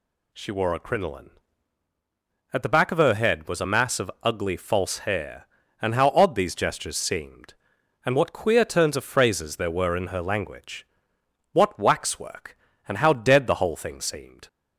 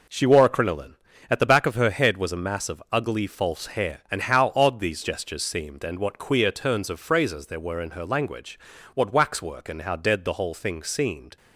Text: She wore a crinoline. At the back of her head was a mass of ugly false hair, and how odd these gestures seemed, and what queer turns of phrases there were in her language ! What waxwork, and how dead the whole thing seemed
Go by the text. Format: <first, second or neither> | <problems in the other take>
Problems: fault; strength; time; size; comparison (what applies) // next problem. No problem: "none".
neither | none